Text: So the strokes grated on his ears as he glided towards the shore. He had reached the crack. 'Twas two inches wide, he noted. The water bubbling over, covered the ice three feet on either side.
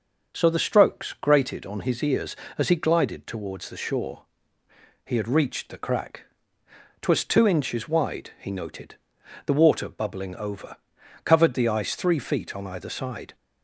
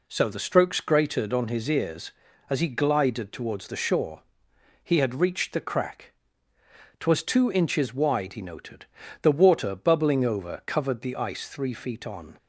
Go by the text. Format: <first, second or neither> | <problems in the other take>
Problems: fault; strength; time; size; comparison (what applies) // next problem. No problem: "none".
first | stops before "either side"; at 12.3 s